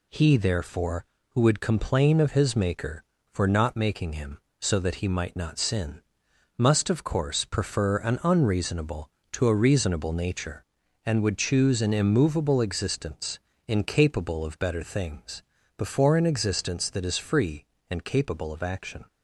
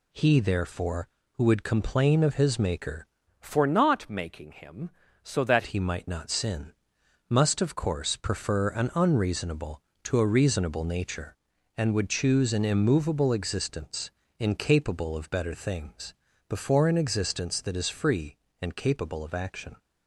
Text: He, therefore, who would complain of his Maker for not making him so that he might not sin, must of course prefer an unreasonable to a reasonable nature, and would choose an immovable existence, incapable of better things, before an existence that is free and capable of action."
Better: first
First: none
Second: changes voice from "for" to "that"; from 3.3 to 5.6 s; 2.3 s long

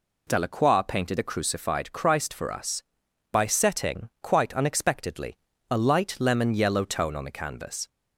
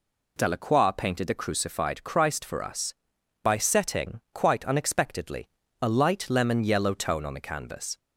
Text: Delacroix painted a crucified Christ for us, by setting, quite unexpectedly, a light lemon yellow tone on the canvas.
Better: neither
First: none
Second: none

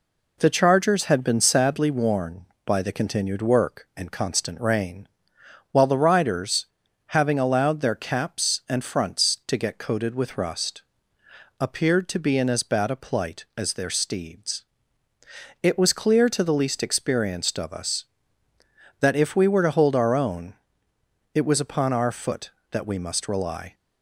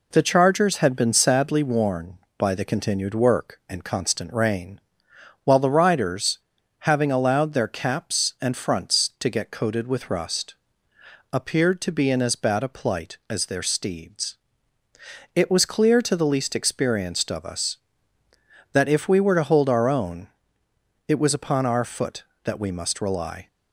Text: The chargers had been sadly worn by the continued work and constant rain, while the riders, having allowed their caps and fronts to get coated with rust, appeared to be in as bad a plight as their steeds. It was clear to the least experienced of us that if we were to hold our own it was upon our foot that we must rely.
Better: neither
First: pauses between "own" and "it"; noticeable; at 20.5 s; 0.80 s long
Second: pauses between "own" and "it"; noticeable; at 20.2 s; 0.80 s long

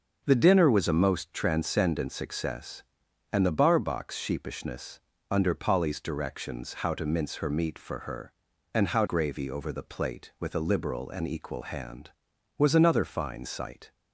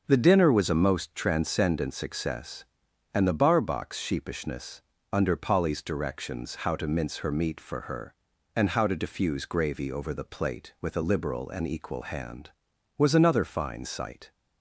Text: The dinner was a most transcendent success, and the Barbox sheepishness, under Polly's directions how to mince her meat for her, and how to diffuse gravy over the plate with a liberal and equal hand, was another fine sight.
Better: second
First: starts louder than the rest; until 1.2 s; 6.5 dB // skips "to diffuse"; at 9.0 s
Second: starts louder than the rest; until 1.0 s; 6.5 dB

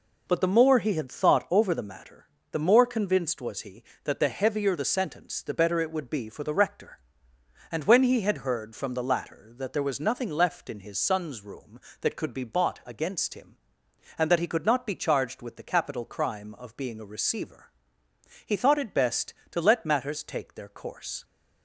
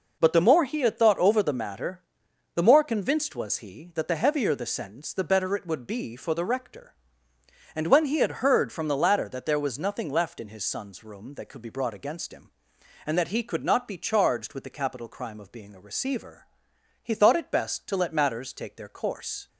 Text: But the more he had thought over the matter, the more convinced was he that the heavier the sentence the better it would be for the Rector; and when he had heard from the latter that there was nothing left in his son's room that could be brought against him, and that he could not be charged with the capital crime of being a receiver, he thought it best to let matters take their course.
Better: second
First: says "bought" for "brought"; at 12.4 s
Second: none

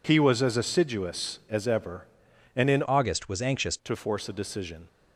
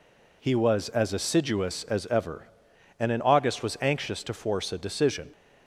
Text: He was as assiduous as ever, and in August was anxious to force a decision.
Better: second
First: changes voice from "August" to "anxious"; from 2.8 to 3.7 s; 0.9 s long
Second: none

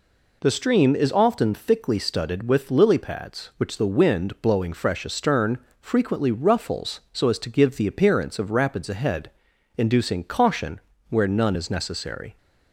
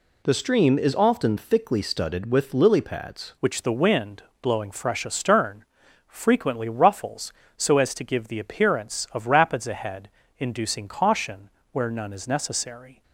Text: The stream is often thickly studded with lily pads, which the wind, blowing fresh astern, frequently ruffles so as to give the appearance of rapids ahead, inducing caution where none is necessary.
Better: first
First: pauses between "caution" and "where"; slight; at 10.7 s; 0.30 s long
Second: changes voice at "which"; from 3.4 s on; 9.6 s long // pauses between "caution" and "where"; slight; at 11.5 s; 0.22 s long

